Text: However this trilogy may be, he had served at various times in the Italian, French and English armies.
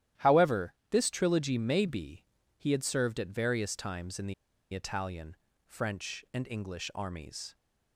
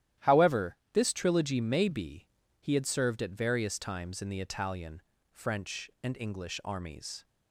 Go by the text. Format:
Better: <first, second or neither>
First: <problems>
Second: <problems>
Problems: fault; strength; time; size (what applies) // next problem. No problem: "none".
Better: second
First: starts louder than the rest; strong; until 1.3 s; 12 dB // pauses between "However" and "this"; slight; at 0.7 s; 0.18 s long // pauses between "the" and "Italian"; at 4.3 s; 0.40 s long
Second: starts louder than the rest; strong; until 1.3 s; 12 dB // pauses between "However" and "this"; slight; at 0.7 s; 0.18 s long